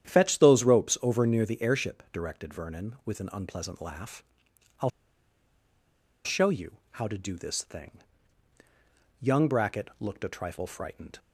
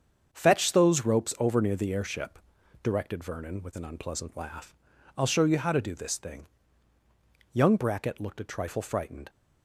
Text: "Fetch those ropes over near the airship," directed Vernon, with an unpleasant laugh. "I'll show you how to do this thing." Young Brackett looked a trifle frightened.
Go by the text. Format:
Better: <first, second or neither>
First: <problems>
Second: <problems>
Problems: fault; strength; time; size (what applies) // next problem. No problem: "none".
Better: second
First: starts louder than the rest; strong; until 1.1 s; 10 dB // pauses between "I'll" and "show"; strong; at 4.8 s; 1.3 s long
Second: starts louder than the rest; strong; until 1.3 s; 7.5 dB